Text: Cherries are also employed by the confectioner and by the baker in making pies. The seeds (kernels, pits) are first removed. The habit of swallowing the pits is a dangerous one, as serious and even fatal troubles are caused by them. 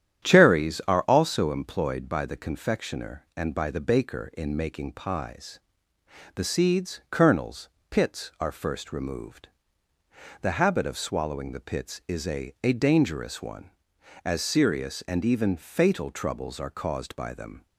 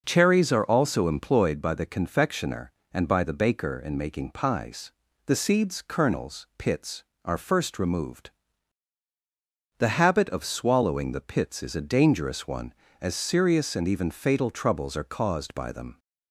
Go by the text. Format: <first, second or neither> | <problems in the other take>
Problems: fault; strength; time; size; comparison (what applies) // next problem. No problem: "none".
second | starts louder than the rest; strong; until 1.3 s; 10 dB // says "a" twice; at 12.6 s